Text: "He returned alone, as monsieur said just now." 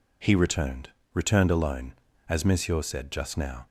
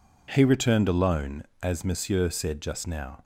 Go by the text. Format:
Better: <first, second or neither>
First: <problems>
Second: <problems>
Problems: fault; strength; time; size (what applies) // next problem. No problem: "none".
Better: second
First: says "returned" twice; at 1.1 s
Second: none